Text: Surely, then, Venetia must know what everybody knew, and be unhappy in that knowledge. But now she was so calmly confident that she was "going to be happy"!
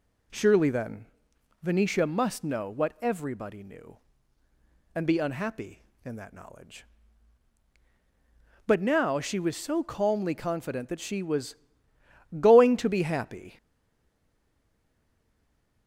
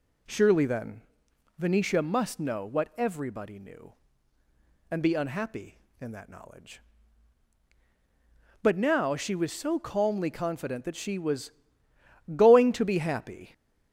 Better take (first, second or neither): second